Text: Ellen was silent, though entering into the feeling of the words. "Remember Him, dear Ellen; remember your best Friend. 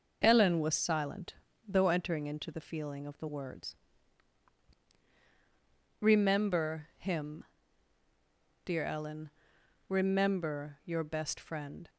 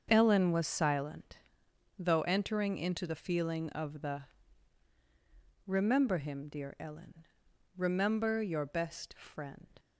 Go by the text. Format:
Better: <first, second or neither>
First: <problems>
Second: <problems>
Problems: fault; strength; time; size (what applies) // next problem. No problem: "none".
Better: first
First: none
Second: starts louder than the rest; until 1.1 s; 6.5 dB // skips "words"; at 4.9 s